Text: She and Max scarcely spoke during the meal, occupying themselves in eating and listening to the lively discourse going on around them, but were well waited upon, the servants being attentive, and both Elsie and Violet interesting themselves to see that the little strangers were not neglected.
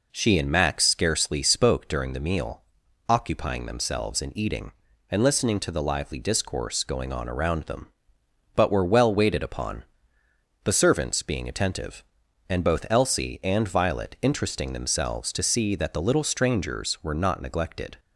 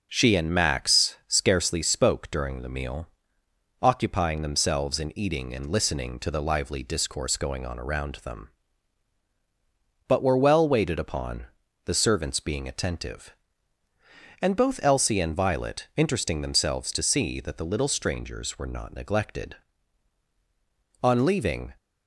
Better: first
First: none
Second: starts louder than the rest; noticeable; until 1.1 s; 6 dB // goes on to say "On leaving"; noticeable; from 21.0 s on; 0.70 s long

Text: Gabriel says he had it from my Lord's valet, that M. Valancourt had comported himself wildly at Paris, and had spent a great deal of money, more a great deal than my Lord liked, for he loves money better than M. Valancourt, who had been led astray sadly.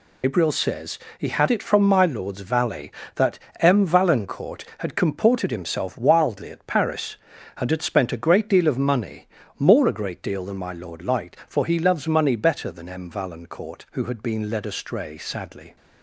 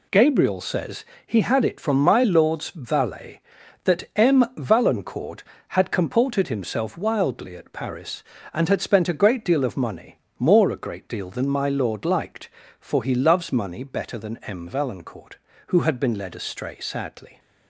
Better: second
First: loses the start of "Gabriel"; at 0.2 s; 150 ms // pauses between "says" and "he"; slight; at 0.9 s; 0.18 s long // pauses between "that" and "M"; slight; at 3.3 s; 0.22 s long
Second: pauses between "says" and "he"; slight; at 1.0 s; 0.22 s long

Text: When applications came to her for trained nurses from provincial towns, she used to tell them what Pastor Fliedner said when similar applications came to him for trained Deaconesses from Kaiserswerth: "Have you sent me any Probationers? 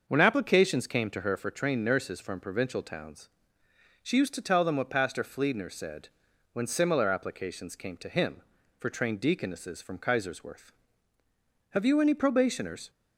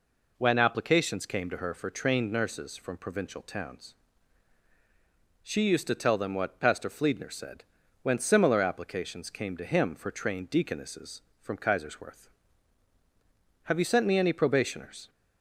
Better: second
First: starts louder than the rest; until 1.0 s; 6.5 dB // pauses between "said" and "when"; noticeable; at 6.0 s; 0.46 s long // skips "sent me"; at 11.9 s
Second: pauses between "said" and "when"; at 7.6 s; 0.38 s long

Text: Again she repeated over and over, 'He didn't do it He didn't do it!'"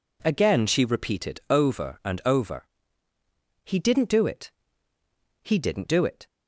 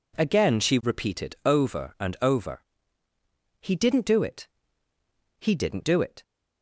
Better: neither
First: pauses between "it" and "He"; noticeable; at 4.5 s; 0.92 s long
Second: pauses between "it" and "He"; noticeable; at 4.4 s; 0.92 s long

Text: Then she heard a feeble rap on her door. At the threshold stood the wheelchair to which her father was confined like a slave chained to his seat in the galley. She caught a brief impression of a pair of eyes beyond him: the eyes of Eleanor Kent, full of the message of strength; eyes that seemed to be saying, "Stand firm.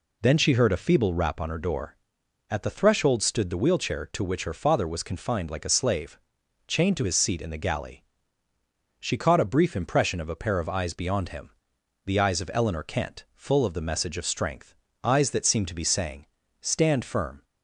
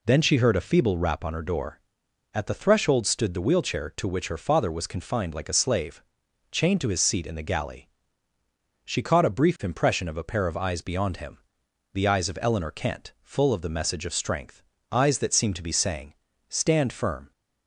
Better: neither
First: pauses between "slave" and "chained"; noticeable; at 6.1 s; 0.48 s long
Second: pauses between "slave" and "chained"; noticeable; at 6.0 s; 0.48 s long

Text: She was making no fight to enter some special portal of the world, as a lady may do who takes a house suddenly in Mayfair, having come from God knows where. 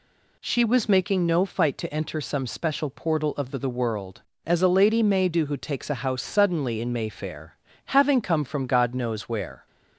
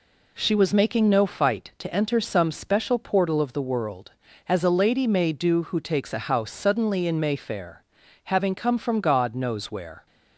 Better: second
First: says "the" twice; at 3.5 s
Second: none

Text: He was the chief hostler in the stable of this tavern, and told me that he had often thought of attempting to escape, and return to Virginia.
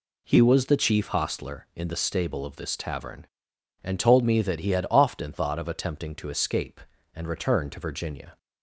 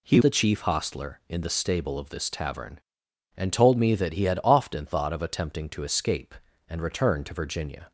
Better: first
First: none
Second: skips "was"; at 0.1 s

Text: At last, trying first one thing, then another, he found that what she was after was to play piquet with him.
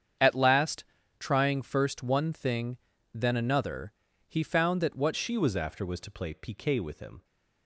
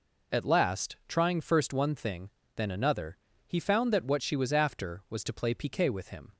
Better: second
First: starts louder than the rest; strong; until 1.5 s; 8.5 dB // changes voice at "she"; from 5.1 s on; 2.1 s long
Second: none

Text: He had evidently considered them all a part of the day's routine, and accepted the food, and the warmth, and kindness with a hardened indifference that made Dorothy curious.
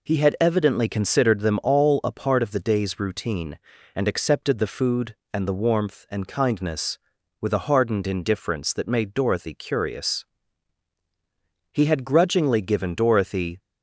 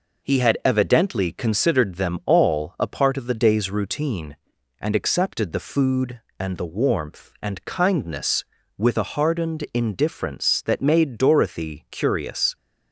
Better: second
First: goes on to say "He had grudgingly given Dorothy"; strong; from 11.7 s on; 1.8 s long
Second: none

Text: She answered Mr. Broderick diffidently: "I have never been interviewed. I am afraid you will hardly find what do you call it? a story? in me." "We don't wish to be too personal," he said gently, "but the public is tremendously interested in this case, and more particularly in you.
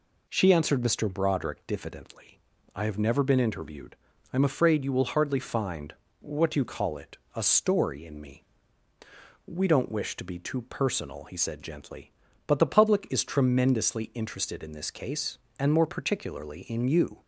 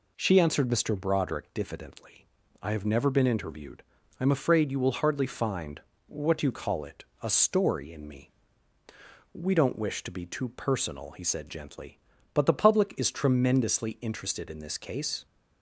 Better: first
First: pauses between "find" and "what"; slight; at 5.9 s; 0.26 s long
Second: pauses between "find" and "what"; slight; at 5.8 s; 0.26 s long // stops before "and more particularly in you"; at 15.2 s

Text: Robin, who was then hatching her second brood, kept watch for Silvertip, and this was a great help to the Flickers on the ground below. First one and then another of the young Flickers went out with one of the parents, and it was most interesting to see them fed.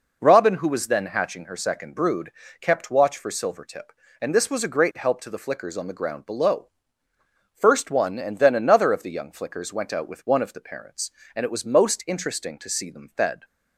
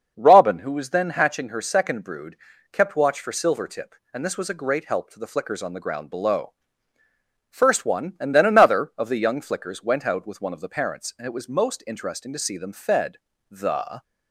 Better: first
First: none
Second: starts louder than the rest; noticeable; until 1.1 s; 6 dB // goes on to say "The"; from 13.5 s on; 0.52 s long

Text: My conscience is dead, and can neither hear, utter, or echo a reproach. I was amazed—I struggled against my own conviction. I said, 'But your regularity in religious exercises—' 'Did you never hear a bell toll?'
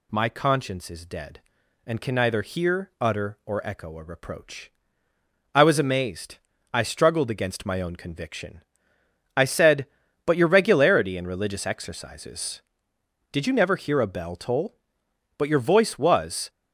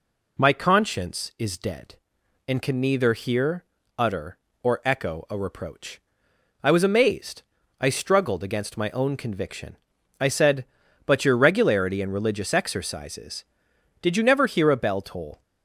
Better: second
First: goes on to say "But your voice was"; noticeable; from 15.3 s on; 1.1 s long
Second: none

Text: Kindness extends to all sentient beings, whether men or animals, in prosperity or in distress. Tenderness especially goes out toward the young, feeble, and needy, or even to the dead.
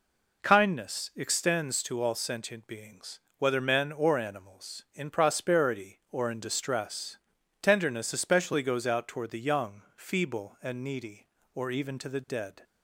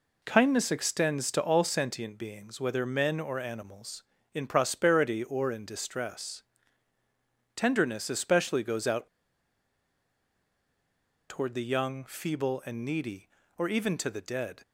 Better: first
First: none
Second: pauses between "out" and "toward"; strong; at 9.0 s; 2.2 s long

